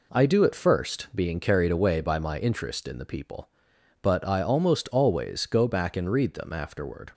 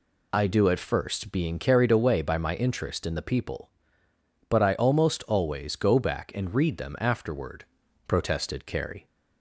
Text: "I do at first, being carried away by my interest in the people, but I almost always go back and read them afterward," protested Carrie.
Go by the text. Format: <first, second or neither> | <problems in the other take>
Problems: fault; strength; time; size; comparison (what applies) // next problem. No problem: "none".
second | stops before "protested Carrie"; at 7.1 s